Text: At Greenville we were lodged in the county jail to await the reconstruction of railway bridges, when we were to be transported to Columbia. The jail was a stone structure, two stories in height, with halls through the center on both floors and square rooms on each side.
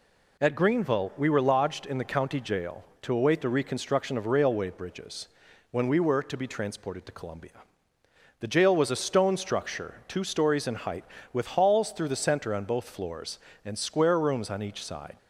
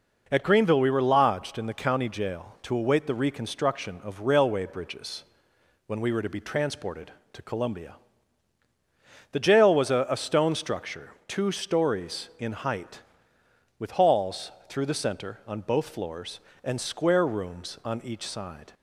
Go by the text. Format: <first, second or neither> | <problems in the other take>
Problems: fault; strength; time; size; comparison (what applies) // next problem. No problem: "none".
first | says "a" twice; at 10.0 s // pauses between "halls" and "through"; slight; at 14.5 s; 0.16 s long